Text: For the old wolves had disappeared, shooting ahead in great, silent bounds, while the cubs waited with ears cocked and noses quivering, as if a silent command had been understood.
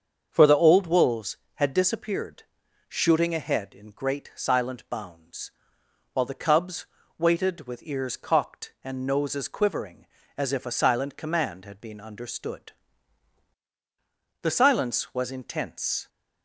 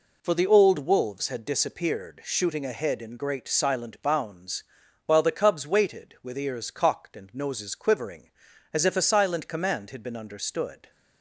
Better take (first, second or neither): second